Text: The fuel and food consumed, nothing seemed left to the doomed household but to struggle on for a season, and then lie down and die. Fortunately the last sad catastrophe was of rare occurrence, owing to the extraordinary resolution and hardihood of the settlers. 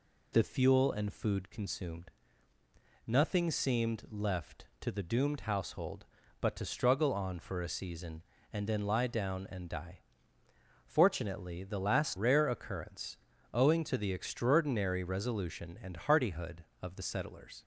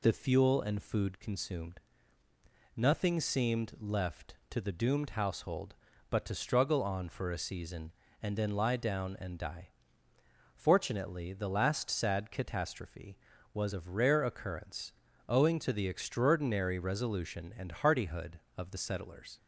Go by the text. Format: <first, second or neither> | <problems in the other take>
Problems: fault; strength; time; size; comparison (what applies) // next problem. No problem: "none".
second | skips "sad catastrophe was of"; at 12.1 s